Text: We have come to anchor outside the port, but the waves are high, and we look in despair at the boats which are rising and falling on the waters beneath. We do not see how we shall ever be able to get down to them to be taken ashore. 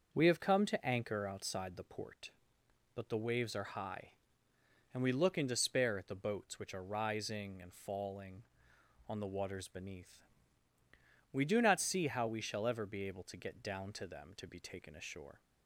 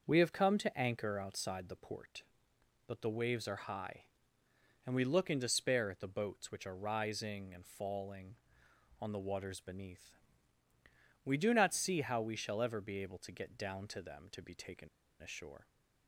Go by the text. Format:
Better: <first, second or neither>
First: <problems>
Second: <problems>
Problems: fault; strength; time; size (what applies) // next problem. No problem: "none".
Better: first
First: starts louder than the rest; until 1.1 s; 6.5 dB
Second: starts louder than the rest; until 1.0 s; 6.5 dB // pauses between "taken" and "ashore"; slight; at 14.8 s; 0.31 s long